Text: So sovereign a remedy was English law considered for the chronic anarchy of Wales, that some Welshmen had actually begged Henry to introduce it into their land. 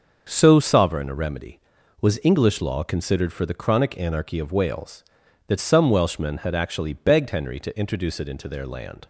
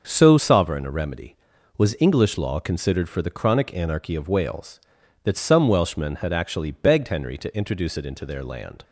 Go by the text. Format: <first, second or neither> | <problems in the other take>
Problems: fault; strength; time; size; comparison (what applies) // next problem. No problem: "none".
neither | starts louder than the rest; the same in both